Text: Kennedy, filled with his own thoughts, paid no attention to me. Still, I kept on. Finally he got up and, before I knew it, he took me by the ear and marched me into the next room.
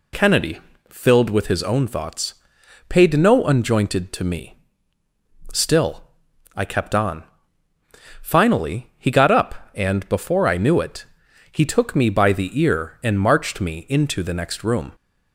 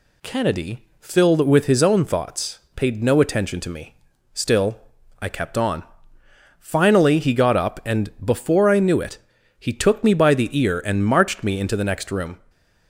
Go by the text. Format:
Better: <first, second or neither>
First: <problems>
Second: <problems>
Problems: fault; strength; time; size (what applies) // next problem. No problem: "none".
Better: second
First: says "unjointed" for "attention"; at 3.4 s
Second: none